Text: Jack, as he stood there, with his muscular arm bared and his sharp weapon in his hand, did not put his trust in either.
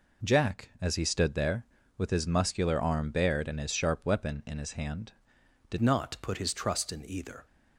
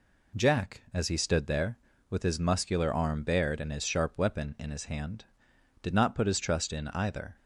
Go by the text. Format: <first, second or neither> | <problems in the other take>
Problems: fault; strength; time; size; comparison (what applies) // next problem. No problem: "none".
second | changes voice at "not"; from 5.8 s on; 1.6 s long